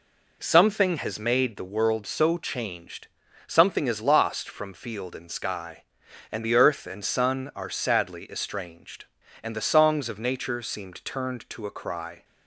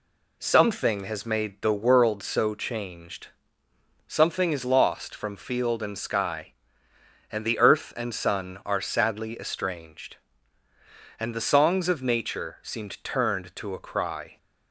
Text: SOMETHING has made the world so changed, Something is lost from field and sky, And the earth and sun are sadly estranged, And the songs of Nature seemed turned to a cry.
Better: neither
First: none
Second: none

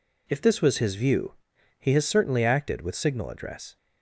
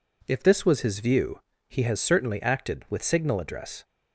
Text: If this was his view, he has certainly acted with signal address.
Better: neither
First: none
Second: none

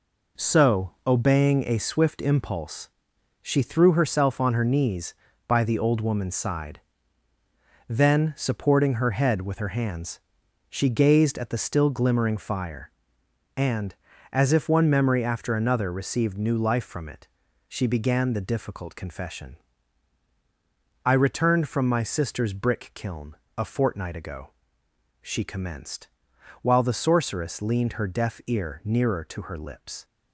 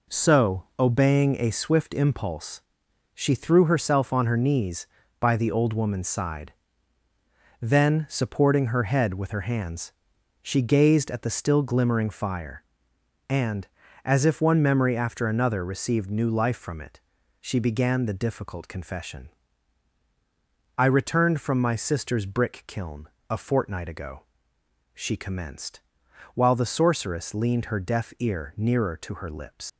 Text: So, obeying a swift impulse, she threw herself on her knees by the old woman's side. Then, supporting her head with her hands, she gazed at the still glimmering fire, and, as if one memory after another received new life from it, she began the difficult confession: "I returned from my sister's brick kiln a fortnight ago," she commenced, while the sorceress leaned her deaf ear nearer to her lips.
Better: first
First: pauses between "kiln" and "a"; slight; at 23.3 s; 0.20 s long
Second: pauses between "kiln" and "a"; slight; at 23.0 s; 0.20 s long // leaves "lips" unfinished; at 29.6 s; 70 ms

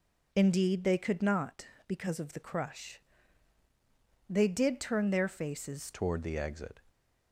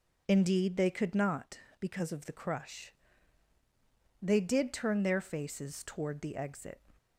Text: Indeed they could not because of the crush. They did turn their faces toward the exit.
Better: second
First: changes voice at "toward"; from 5.9 s on; 0.8 s long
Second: none

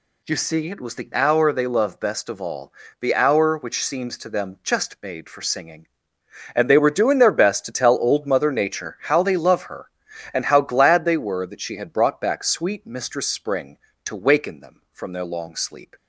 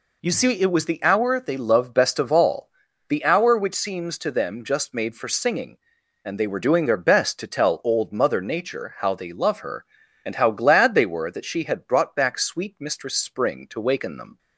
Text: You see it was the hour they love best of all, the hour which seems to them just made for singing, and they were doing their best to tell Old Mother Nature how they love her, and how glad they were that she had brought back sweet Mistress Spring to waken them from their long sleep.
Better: first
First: none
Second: stops before "from their long sleep"; at 14.3 s

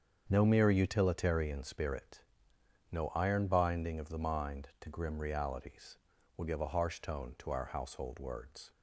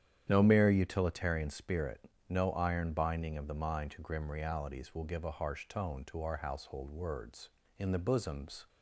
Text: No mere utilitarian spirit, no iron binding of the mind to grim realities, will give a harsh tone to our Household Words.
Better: first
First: starts louder than the rest; strong; until 1.3 s; 7 dB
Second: starts louder than the rest; strong; until 1.2 s; 9.5 dB // goes on to say "In the bosoms"; noticeable; from 7.7 s on; 0.90 s long

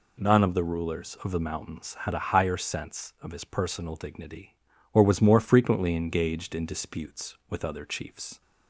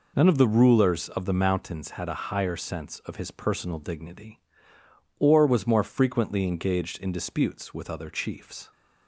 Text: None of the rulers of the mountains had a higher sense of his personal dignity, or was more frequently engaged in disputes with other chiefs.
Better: neither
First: none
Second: none

